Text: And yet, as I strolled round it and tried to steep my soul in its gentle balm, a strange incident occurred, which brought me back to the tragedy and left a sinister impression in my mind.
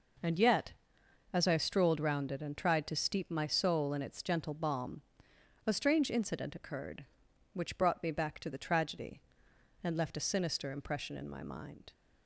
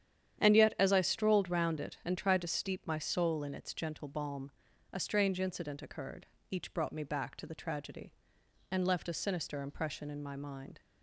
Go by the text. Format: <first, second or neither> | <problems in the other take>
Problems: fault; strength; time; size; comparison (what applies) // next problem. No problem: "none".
first | starts louder than the rest; strong; until 1.4 s; 9.5 dB // says "each" for "which"; at 6.5 s